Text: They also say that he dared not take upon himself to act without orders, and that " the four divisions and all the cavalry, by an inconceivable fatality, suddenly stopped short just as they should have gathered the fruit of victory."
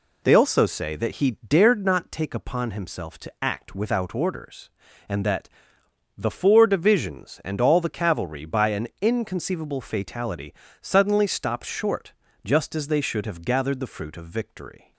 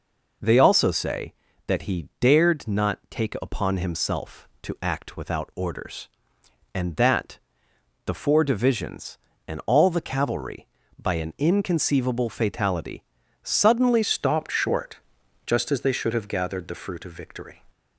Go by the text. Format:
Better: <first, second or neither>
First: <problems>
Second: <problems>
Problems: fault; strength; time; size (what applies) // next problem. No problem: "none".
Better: first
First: pauses between "short" and "just"; slight; at 12.1 s; 0.32 s long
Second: changes voice at "stopped"; from 14.0 s on; 3.6 s long // pauses between "short" and "just"; noticeable; at 14.9 s; 0.48 s long